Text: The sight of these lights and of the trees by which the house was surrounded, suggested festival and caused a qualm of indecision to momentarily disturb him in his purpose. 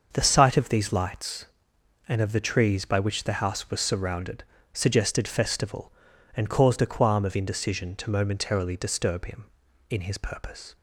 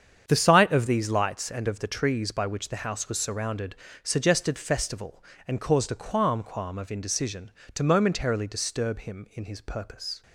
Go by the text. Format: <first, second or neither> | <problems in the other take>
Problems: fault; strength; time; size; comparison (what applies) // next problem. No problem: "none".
first | starts louder than the rest; strong; until 1.2 s; 8 dB; also in the first // says "qualm" twice; at 6.4 s